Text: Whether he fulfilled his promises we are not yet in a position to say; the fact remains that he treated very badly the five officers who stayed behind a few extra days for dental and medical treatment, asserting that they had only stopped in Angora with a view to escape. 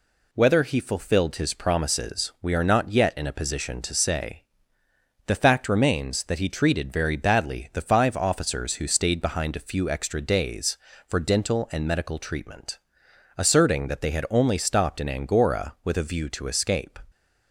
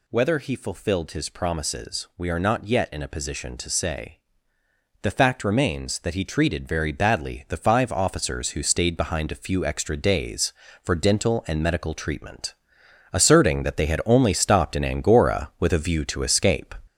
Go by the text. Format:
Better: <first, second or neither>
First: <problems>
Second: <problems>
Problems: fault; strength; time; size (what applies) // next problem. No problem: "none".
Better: first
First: none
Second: gets louder; noticeable; throughout; 5.5 dB